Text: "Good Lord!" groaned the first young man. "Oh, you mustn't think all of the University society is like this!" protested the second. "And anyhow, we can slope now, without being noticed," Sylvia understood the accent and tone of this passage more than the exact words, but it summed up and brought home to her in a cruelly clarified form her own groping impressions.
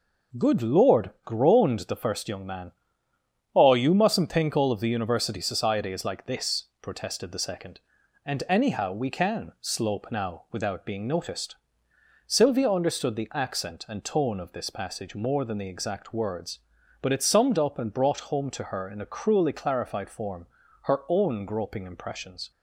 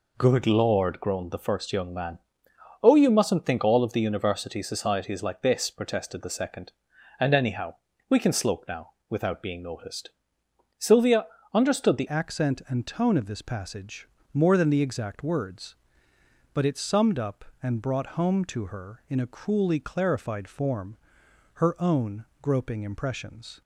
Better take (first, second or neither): first